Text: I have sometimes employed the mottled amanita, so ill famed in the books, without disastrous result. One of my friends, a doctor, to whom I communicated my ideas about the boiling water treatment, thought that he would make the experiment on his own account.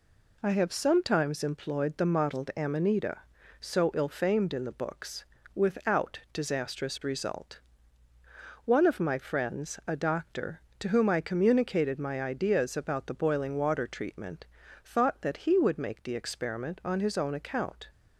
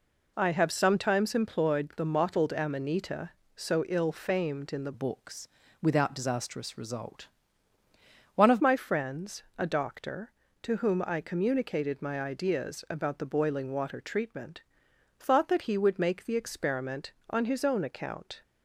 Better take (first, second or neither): first